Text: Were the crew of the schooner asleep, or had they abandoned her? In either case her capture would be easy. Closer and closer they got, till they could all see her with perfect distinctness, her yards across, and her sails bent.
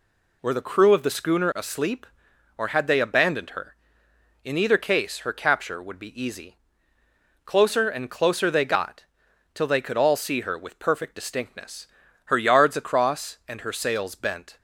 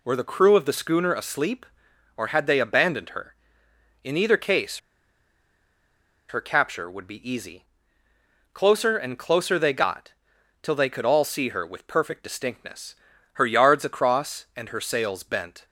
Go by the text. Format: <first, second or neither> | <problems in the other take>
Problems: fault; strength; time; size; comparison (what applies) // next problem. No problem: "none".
first | pauses between "case" and "her"; strong; at 4.7 s; 1.5 s long